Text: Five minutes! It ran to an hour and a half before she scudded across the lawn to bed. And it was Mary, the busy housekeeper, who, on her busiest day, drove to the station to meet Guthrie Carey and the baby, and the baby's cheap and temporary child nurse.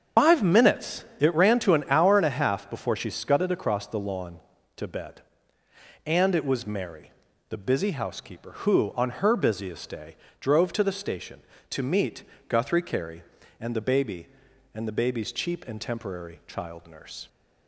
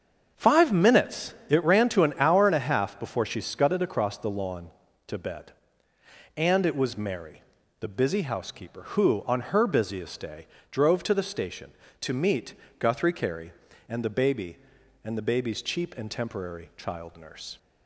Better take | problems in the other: second | loses the start of "Five"; at 0.1 s; 105 ms // starts louder than the rest; strong; until 1.3 s; 7.5 dB; also in the second // pauses between "meet" and "Guthrie"; slight; at 12.2 s; 0.26 s long; slight in the second

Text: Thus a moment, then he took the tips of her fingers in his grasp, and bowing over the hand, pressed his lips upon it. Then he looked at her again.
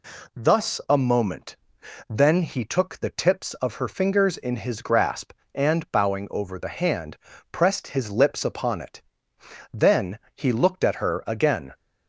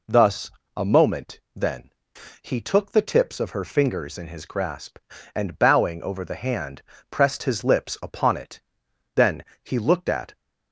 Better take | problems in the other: first | pauses between "Thus" and "a"; slight; at 0.5 s; 0.26 s long // pauses between "then" and "he"; noticeable; at 1.8 s; 0.54 s long // pauses between "Then" and "he"; slight; at 9.4 s; 0.20 s long; slight in the first // stops before "her again"; at 10.3 s

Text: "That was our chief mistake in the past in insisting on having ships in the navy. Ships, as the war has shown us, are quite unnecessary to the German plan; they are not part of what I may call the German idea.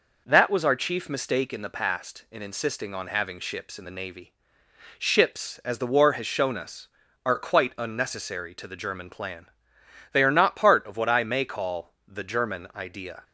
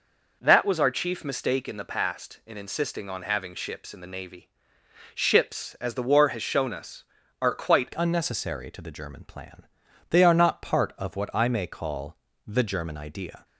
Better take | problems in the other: first | changes voice at "unnecessary"; from 7.9 s on; 5.5 s long // pauses between "call" and "the"; slight; at 12.1 s; 0.28 s long

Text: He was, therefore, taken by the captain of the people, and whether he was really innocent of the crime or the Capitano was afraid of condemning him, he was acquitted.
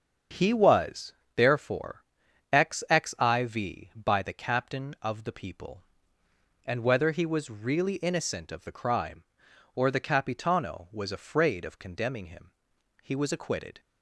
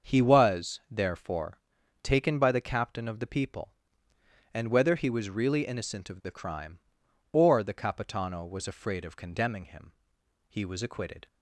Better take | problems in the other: second | starts louder than the rest; until 1.5 s; 7 dB; also in the second // says "xxiv" for "taken"; at 2.5 s

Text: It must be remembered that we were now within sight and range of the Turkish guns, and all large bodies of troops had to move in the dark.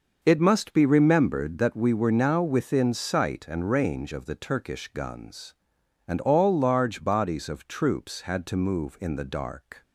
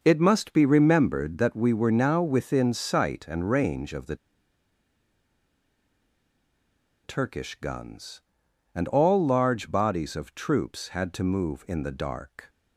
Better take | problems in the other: first | pauses between "the" and "Turkish"; strong; at 4.1 s; 2.8 s long

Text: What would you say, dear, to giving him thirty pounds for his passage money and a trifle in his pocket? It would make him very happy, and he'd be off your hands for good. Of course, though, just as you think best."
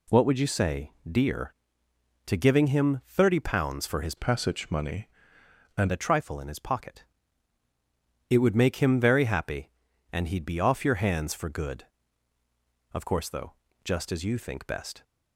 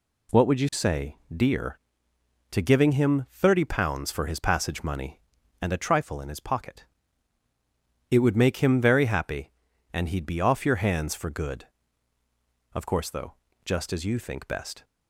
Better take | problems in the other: second | changes voice from "passage" to "and"; from 4.1 to 5.9 s; 1.8 s long

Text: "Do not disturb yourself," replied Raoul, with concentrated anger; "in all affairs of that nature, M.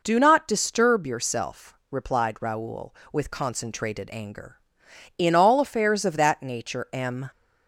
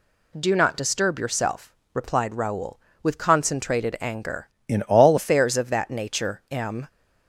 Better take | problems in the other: first | changes voice from "in" to "all"; from 4.6 to 5.1 s; 0.5 s long

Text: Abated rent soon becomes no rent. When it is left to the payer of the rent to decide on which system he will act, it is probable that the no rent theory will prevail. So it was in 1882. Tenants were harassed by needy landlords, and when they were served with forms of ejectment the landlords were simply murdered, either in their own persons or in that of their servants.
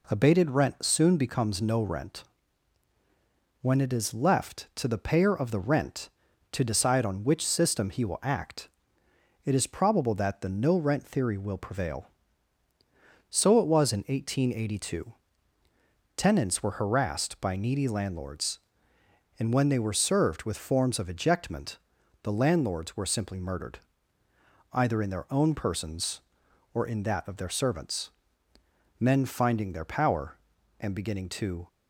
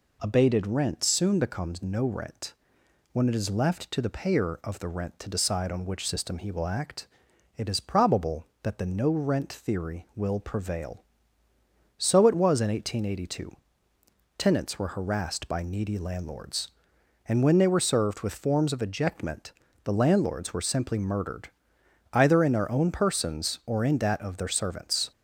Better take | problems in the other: second | pauses between "ejectment" and "the"; at 21.7 s; 0.44 s long; slight in the second // goes on to say "Men finding their power and beginning to"; strong; from 28.9 s on; 2.6 s long

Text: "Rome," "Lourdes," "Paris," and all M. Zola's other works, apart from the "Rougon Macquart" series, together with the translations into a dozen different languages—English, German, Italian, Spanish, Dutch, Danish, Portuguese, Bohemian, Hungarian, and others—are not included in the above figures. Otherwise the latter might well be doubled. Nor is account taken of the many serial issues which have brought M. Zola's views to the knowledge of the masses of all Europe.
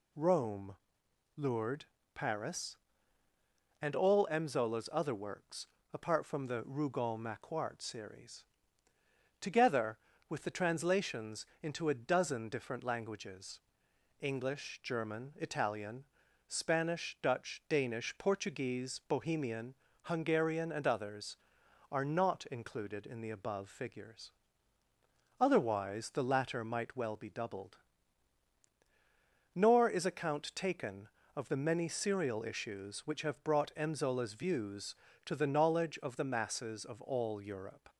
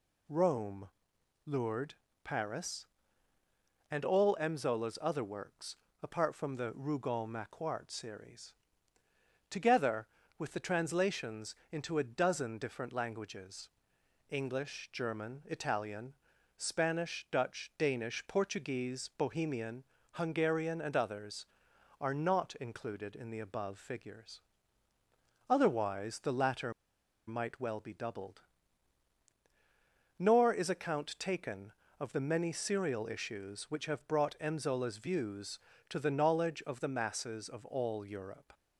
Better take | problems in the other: first | pauses between "translations" and "into"; slight; at 11.5 s; 0.16 s long; slight in the first // pauses between "latter" and "might"; noticeable; at 26.7 s; 0.55 s long

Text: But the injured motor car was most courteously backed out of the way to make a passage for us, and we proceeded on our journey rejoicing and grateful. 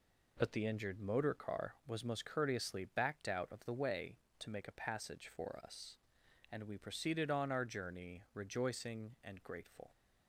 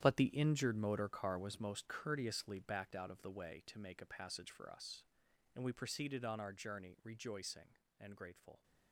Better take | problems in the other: first | gets quieter; strong; throughout; 12.5 dB

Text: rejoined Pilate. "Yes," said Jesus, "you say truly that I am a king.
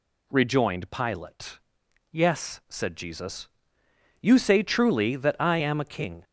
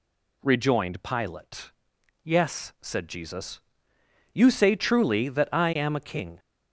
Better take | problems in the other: neither | none

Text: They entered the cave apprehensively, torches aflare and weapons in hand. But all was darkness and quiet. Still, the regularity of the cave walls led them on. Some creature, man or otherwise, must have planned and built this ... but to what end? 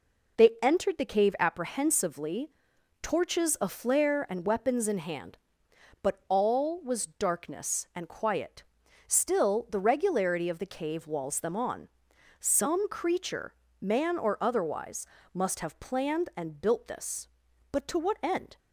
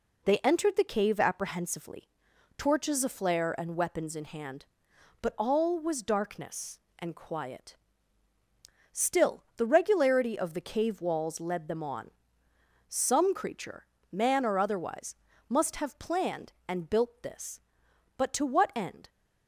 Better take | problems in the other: second | skips "led"; at 11.3 s

